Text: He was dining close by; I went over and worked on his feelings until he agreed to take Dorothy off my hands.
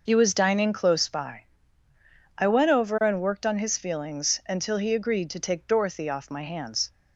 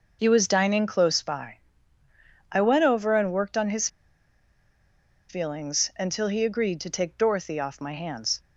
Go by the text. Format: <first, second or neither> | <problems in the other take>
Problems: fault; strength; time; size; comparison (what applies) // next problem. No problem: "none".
first | pauses between "his" and "feelings"; strong; at 3.8 s; 1.4 s long